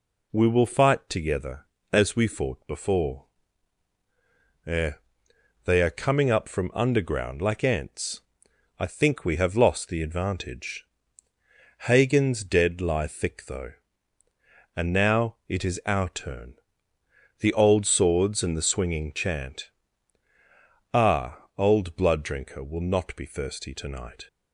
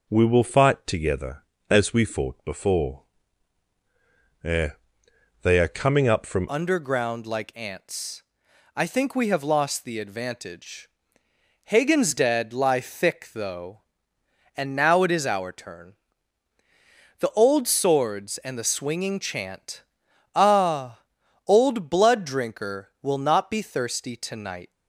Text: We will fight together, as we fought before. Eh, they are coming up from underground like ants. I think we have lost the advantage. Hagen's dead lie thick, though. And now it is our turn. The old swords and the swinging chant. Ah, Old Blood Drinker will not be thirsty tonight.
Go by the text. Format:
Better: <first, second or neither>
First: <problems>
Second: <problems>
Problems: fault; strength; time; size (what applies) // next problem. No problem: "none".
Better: first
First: none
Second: changes voice at "underground"; from 6.4 s on; 18.3 s long